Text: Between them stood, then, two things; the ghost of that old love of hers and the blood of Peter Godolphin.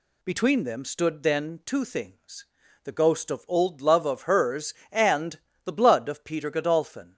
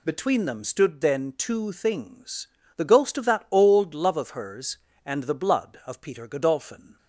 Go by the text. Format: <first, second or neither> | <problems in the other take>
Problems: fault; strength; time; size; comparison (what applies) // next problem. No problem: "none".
second | skips "that"; at 3.4 s // pauses between "and" and "the"; slight; at 5.3 s; 0.24 s long